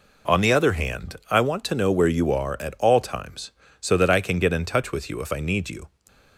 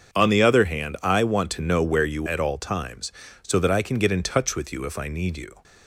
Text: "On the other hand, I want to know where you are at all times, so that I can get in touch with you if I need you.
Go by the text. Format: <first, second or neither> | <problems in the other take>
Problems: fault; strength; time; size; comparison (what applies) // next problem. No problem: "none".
first | starts louder than the rest; until 1.1 s; 6.5 dB // skips "are"; at 2.2 s